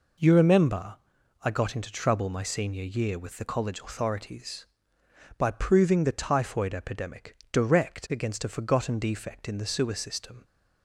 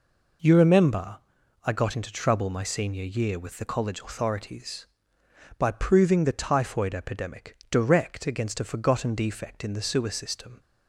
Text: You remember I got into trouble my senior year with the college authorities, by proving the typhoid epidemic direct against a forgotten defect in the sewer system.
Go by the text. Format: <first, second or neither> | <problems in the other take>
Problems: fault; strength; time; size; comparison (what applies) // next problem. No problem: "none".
neither | pauses between "remember" and "I"; noticeable; the same in both // pauses between "epidemic" and "direct"; slight; the same in both